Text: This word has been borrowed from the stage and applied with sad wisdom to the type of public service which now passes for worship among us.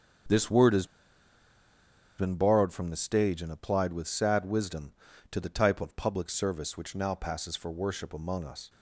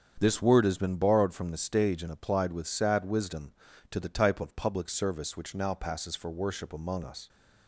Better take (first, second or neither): second